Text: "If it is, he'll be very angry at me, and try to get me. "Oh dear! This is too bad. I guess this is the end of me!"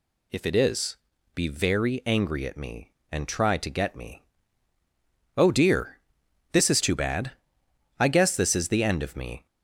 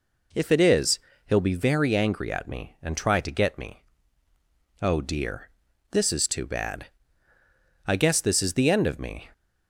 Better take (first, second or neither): second